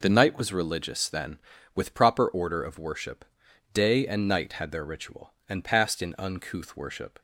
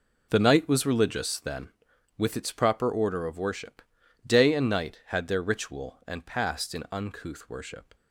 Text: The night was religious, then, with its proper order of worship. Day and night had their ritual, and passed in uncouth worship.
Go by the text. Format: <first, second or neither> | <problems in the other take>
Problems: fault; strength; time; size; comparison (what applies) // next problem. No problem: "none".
second | skips "its"; at 1.9 s